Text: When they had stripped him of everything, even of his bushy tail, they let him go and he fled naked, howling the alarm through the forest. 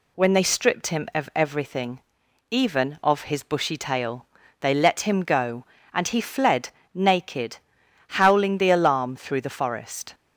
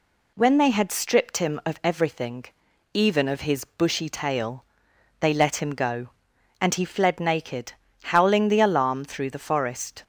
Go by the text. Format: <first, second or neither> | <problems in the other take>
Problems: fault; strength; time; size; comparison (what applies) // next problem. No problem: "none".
second | skips "had"; at 0.4 s // pauses between "fled" and "naked"; slight; at 6.6 s; 0.26 s long